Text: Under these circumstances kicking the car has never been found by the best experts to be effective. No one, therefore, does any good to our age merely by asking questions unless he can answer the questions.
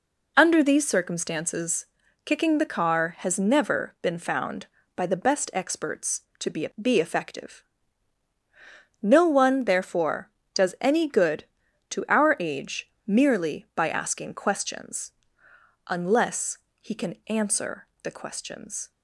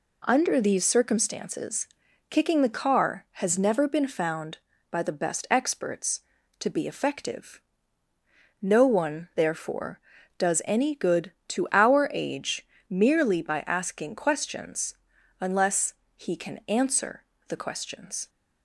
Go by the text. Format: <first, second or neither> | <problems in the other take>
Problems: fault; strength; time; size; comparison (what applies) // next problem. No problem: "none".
second | pauses between "circumstances" and "kicking"; at 1.8 s; 0.38 s long; also in the second // says "be" twice; at 6.8 s // pauses between "age" and "merely"; slight; at 12.8 s; 0.16 s long; slight in the second // pauses between "questions" and "unless"; noticeable; at 15.1 s; 0.76 s long; also in the second // pauses between "unless" and "he"; slight; at 16.5 s; 0.20 s long; slight in the second // pauses between "answer" and "the"; slight; at 17.8 s; 0.16 s long; slight in the second